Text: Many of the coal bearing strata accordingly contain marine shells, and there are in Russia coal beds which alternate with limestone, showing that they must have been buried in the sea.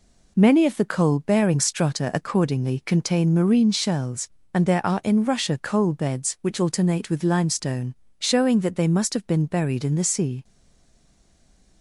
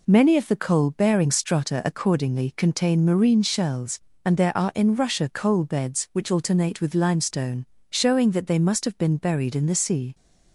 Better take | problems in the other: second | stays silent after the last word; noticeable; from 10.4 s on; 1.4 s long

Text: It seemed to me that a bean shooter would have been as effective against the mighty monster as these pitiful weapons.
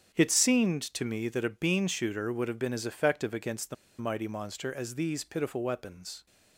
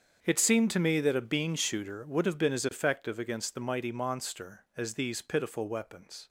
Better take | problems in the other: second | starts louder than the rest; strong; until 1.2 s; 8.5 dB; strong in the second // pauses between "the" and "mighty"; slight; at 3.7 s; 0.24 s long

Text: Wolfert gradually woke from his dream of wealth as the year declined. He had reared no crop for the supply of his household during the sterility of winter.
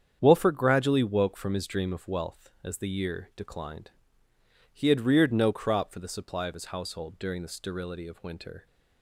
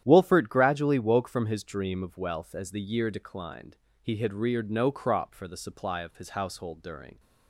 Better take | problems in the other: first | starts louder than the rest; strong; until 1.0 s; 10.5 dB; strong in the first // stops before "the sterility of winter"; at 7.1 s

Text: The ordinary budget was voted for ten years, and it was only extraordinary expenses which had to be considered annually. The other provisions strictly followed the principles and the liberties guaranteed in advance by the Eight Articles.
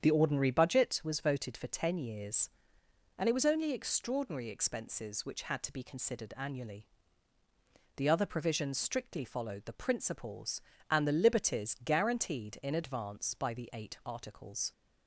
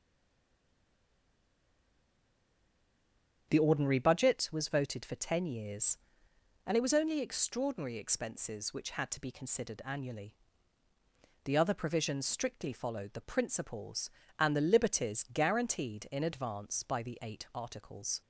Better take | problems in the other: first | stays silent before the first word; strong; until 3.4 s; 3.4 s long // starts louder than the rest; strong; until 4.5 s; 8 dB; strong in the first

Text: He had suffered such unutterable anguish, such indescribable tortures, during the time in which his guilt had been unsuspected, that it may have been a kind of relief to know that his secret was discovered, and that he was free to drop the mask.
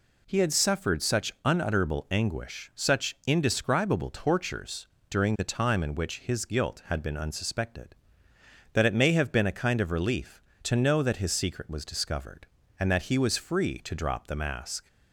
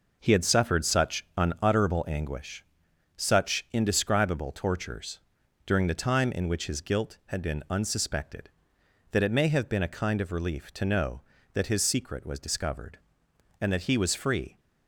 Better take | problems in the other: first | stops before "to drop the mask"; at 14.5 s

